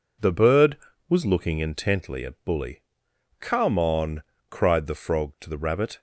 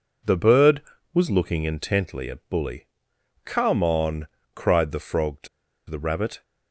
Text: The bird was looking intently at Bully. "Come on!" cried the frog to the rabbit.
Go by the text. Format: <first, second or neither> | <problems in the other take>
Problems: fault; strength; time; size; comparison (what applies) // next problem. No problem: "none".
first | pauses between "to" and "the"; at 5.4 s; 0.41 s long